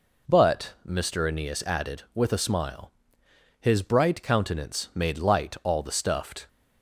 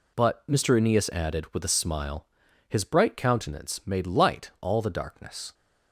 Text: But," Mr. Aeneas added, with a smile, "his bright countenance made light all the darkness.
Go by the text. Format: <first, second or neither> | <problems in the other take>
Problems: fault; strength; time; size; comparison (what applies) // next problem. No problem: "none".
second | says "stuffed" for "darkness"; at 5.9 s